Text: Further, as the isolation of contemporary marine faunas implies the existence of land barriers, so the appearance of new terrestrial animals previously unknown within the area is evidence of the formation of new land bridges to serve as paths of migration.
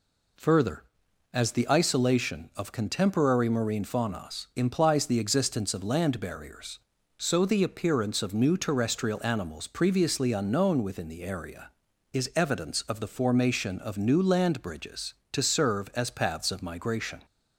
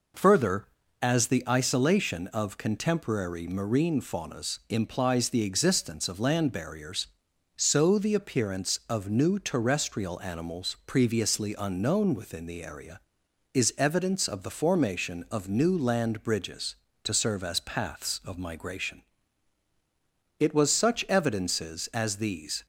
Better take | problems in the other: first | goes on to say "It was such evidences as these"; strong; from 20.3 s on; 2.2 s long

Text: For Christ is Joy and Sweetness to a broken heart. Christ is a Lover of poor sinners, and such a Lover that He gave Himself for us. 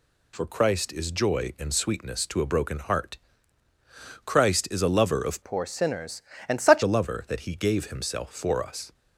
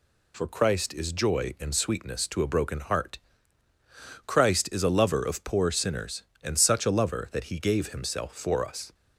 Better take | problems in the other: second | changes voice from "poor" to "such"; from 5.4 to 6.8 s; 1.4 s long

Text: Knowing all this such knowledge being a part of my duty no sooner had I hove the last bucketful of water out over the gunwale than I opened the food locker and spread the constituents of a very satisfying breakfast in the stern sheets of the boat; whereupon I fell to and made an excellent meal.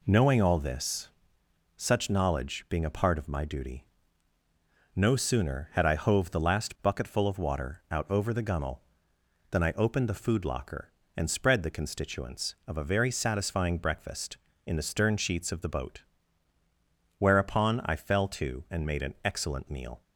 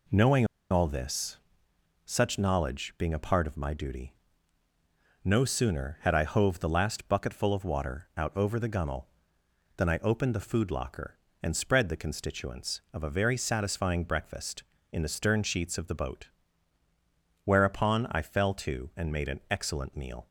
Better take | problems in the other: first | pauses between "Knowing" and "all"; slight; at 0.4 s; 0.25 s long // pauses between "this" and "such"; noticeable; at 1.3 s; 0.70 s long; noticeable in the first // pauses between "duty" and "no"; at 4.1 s; 1.1 s long; also in the first

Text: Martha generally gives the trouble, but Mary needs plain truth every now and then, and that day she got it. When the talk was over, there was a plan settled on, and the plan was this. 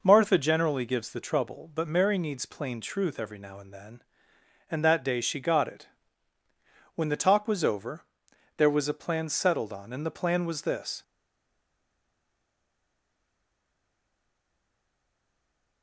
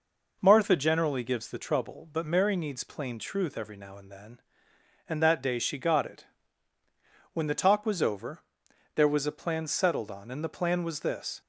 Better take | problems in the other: second | stays silent after the last word; strong; from 11.0 s on; 4.8 s long

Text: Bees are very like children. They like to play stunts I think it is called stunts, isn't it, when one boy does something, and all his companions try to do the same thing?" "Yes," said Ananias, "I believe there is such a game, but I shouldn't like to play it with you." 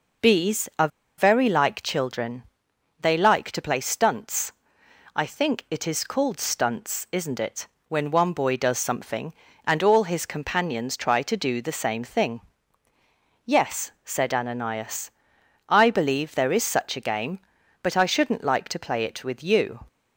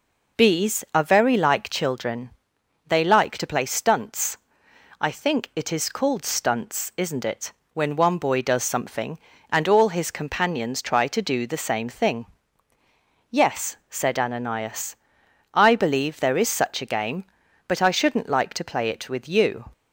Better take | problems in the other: second | pauses between "are" and "very"; slight; at 0.8 s; 0.30 s long // pauses between "stunts" and "I"; noticeable; at 4.5 s; 0.60 s long; noticeable in the second

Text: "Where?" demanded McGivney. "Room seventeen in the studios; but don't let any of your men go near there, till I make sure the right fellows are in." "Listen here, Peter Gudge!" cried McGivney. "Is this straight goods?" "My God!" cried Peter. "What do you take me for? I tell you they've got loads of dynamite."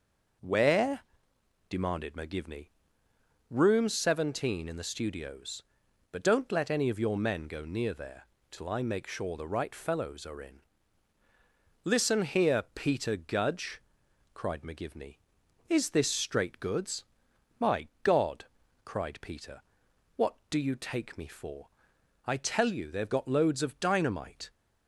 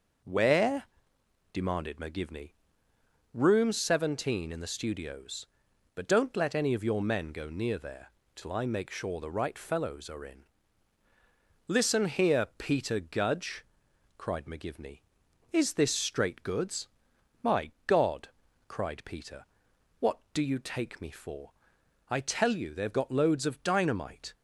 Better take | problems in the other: neither | pauses between "My" and "God"; slight; the same in both

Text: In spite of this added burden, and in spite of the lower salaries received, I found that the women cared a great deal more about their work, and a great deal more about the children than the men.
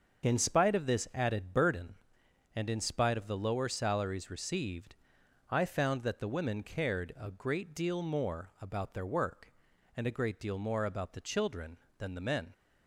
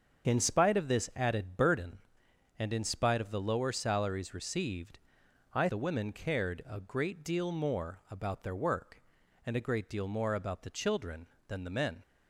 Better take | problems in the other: first | starts louder than the rest; until 1.3 s; 7 dB; also in the first // skips "found that"; at 5.6 s

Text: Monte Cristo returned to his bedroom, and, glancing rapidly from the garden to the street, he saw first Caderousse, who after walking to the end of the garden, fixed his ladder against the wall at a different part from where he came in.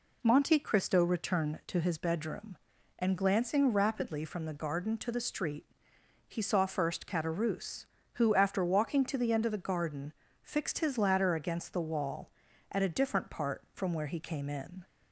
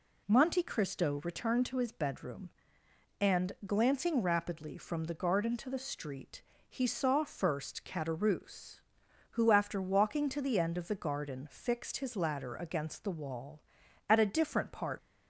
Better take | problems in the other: first | stops before "from where he came in"; at 14.9 s

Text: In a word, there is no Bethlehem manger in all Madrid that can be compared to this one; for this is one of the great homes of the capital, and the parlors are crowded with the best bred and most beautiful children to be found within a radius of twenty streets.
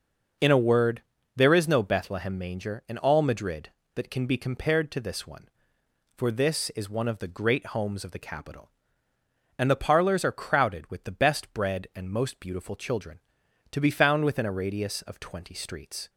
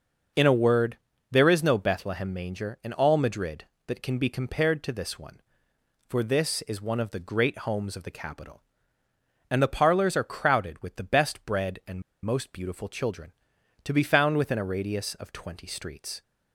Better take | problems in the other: first | pauses between "and" and "most"; slight; at 12.0 s; 0.21 s long

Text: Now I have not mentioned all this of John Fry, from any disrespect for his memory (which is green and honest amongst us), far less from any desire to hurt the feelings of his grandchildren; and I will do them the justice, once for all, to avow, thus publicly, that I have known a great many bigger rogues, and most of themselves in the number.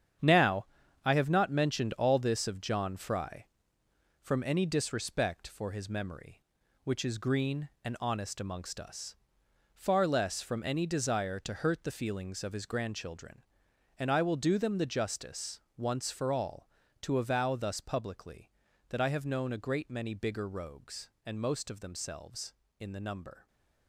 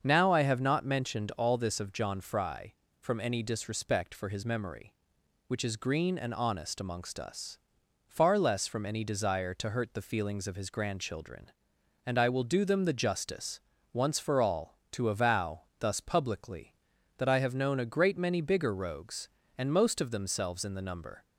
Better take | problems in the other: second | gets quieter; strong; throughout; 9 dB // starts louder than the rest; strong; until 1.6 s; 8.5 dB; also in the second // pauses between "Now" and "I"; at 0.6 s; 0.40 s long

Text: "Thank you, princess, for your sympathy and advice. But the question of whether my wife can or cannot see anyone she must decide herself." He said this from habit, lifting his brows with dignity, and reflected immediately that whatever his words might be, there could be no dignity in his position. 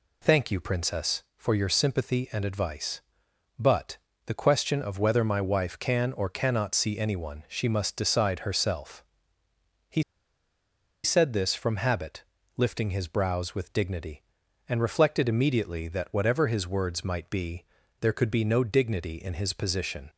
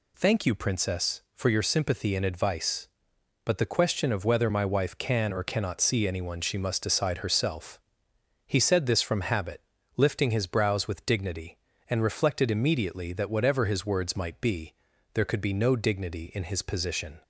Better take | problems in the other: second | pauses between "But" and "the"; slight; at 3.9 s; 0.30 s long // pauses between "He" and "said"; at 10.0 s; 1.0 s long

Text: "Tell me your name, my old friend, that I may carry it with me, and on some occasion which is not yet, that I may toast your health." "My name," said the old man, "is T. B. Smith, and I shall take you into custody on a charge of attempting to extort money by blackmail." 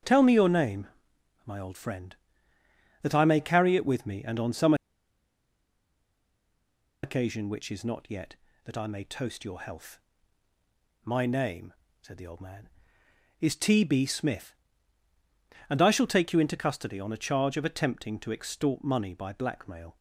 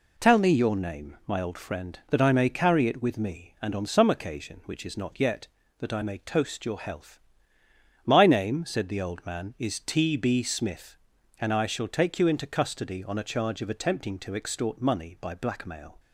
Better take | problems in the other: second | starts louder than the rest; strong; until 1.6 s; 7.5 dB // pauses between "some" and "occasion"; strong; at 4.7 s; 2.2 s long

